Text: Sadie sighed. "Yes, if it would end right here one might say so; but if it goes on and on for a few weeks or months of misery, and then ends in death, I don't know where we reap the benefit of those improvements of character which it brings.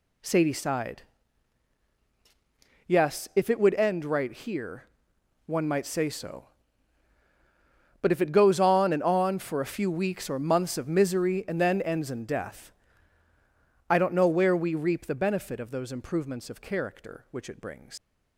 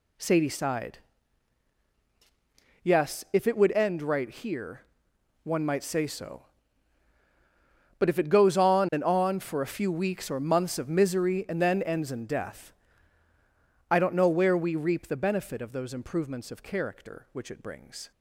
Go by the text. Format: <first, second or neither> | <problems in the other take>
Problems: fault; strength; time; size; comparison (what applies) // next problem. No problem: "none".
second | pauses between "here" and "one"; noticeable; at 4.8 s; 0.62 s long; noticeable in the second // leaves "brings" unfinished; at 17.9 s; 115 ms